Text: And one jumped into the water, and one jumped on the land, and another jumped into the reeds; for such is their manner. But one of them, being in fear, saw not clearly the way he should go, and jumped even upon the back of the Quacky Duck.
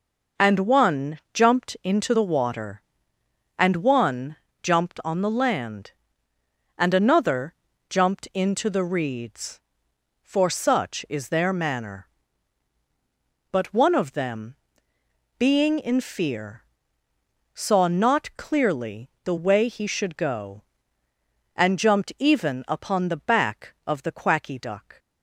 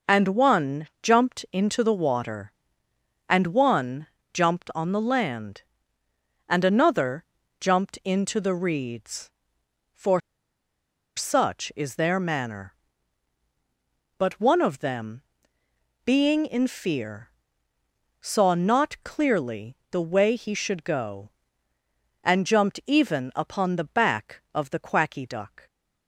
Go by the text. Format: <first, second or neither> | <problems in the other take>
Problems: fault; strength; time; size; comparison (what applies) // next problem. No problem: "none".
first | pauses between "one" and "jumped"; slight; at 4.0 s; 0.28 s long; slight in the first // pauses between "another" and "jumped"; slight; at 7.2 s; 0.34 s long; slight in the first // pauses between "for" and "such"; noticeable; at 10.1 s; 0.96 s long // pauses between "clearly" and "the"; slight; at 19.7 s; 0.16 s long; slight in the first